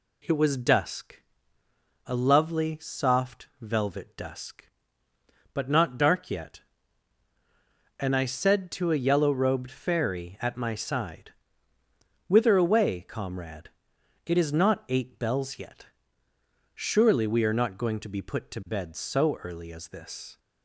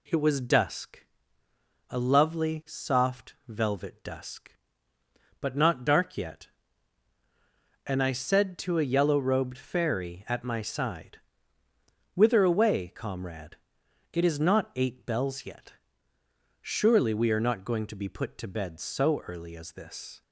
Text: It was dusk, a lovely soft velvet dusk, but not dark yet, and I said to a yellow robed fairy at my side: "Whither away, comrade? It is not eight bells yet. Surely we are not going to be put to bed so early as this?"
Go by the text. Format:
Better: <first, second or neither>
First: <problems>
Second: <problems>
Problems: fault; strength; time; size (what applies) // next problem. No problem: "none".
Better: neither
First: none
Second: none